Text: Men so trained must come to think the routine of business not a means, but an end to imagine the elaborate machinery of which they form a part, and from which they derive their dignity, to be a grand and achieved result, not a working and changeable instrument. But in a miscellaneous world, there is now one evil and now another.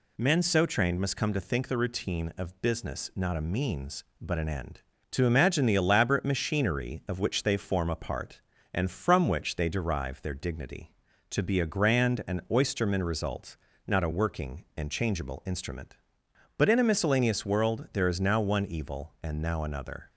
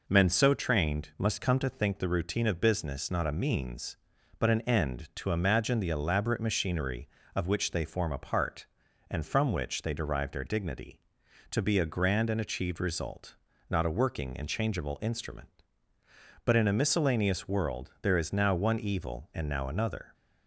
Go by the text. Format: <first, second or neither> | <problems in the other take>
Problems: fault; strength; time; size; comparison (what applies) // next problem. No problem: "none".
second | says "oysterman" for "achieved"; at 12.4 s